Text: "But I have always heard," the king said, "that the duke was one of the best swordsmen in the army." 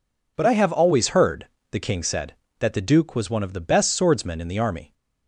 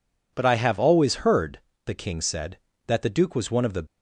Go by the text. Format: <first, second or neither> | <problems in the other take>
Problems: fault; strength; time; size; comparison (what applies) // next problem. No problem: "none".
first | stops before "best swordsmen in the army"; at 3.8 s